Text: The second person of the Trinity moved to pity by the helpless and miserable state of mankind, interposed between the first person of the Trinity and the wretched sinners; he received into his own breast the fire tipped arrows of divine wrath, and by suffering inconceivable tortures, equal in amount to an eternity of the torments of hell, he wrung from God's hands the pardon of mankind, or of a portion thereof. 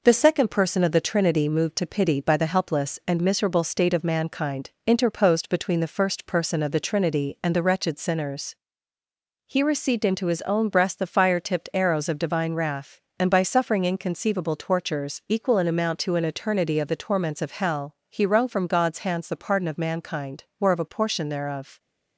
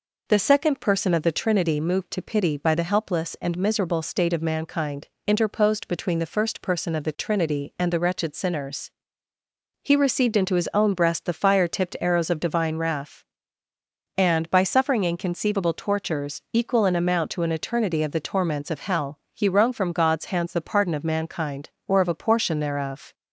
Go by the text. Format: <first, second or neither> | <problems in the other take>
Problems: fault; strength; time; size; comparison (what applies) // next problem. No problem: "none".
second | gets quieter; slight; throughout; 3.5 dB